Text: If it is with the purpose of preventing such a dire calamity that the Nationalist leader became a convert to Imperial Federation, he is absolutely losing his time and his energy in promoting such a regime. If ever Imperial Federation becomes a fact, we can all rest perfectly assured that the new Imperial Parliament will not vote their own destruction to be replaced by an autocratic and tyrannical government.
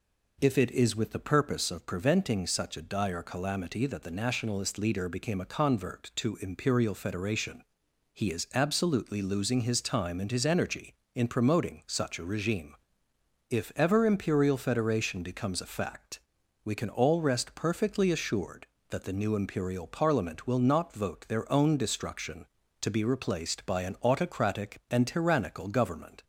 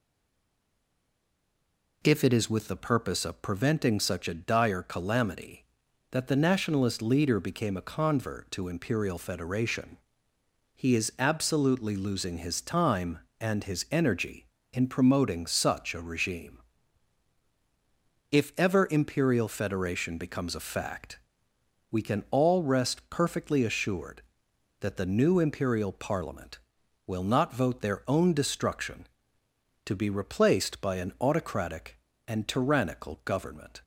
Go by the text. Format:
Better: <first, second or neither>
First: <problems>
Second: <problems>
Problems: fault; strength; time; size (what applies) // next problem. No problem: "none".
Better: first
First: none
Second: stays silent before the first word; noticeable; until 2.0 s; 2.0 s long